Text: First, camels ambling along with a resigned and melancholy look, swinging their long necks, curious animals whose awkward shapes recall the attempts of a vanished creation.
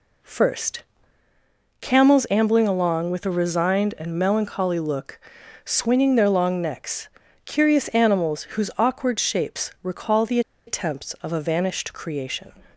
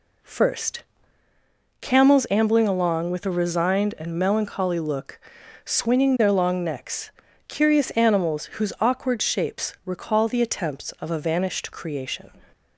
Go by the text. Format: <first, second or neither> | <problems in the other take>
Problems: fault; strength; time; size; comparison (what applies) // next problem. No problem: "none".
second | pauses between "the" and "attempts"; slight; at 10.3 s; 0.27 s long